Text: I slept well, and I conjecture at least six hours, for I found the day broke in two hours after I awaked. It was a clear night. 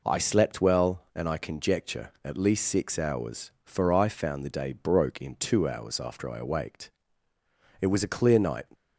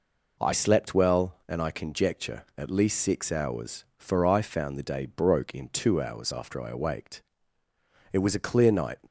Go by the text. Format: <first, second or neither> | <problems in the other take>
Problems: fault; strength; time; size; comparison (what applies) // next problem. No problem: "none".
neither | none